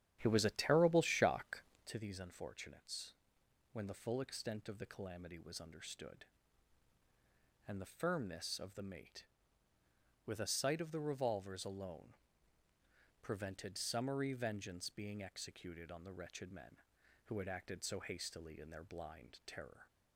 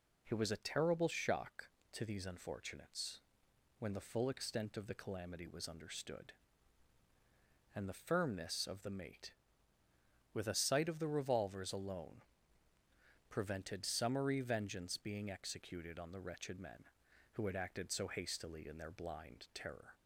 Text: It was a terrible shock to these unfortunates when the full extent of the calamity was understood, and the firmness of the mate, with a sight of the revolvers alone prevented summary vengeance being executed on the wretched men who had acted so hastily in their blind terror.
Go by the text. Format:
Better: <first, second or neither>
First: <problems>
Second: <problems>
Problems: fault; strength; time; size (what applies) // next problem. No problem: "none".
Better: second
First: starts louder than the rest; strong; until 1.9 s; 10 dB // pauses between "unfortunates" and "when"; noticeable; at 3.1 s; 0.58 s long // pauses between "alone" and "prevented"; at 12.1 s; 1.0 s long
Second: pauses between "unfortunates" and "when"; noticeable; at 3.1 s; 0.58 s long // pauses between "alone" and "prevented"; at 12.2 s; 1.0 s long